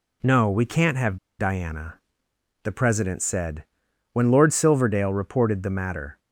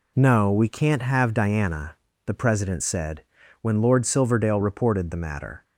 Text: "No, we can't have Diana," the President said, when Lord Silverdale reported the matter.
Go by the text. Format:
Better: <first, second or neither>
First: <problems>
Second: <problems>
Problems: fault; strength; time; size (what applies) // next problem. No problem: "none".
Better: second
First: pauses between "have" and "Diana"; slight; at 1.1 s; 0.23 s long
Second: none